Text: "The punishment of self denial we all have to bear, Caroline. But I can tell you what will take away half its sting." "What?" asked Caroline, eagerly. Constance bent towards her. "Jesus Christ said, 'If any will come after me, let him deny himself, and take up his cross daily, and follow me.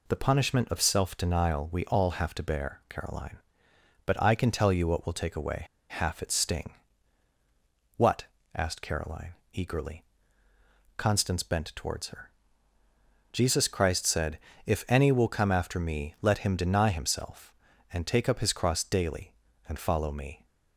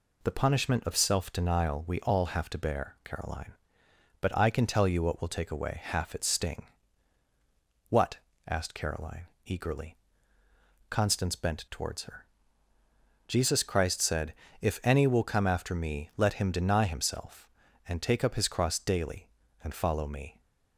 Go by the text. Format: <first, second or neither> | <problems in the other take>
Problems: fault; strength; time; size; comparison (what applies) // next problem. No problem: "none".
second | pauses between "away" and "half"; slight; at 5.6 s; 0.25 s long